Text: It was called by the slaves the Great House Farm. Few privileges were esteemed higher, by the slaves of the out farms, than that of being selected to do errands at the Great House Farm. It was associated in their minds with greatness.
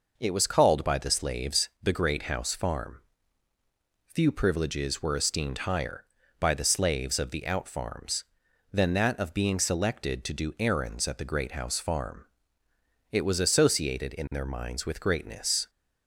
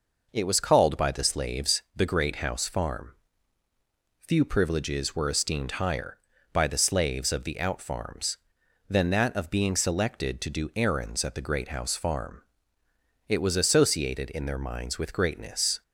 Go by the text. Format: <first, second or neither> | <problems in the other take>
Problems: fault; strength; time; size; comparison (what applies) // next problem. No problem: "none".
neither | pauses between "slaves" and "the"; slight; the same in both